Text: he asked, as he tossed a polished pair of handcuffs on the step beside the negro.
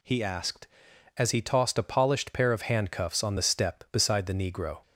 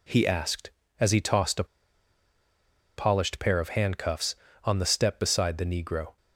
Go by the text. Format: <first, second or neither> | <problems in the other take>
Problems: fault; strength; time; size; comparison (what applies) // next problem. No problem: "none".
first | pauses between "a" and "polished"; strong; at 1.6 s; 1.3 s long